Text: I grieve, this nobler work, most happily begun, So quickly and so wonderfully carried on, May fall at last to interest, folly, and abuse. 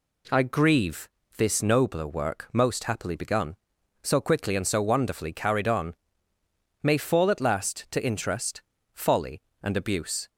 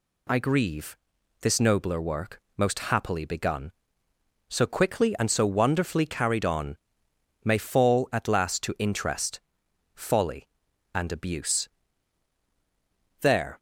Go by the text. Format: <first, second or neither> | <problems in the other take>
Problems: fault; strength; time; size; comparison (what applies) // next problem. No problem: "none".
first | goes on to say "There"; slight; from 13.2 s on; 0.36 s long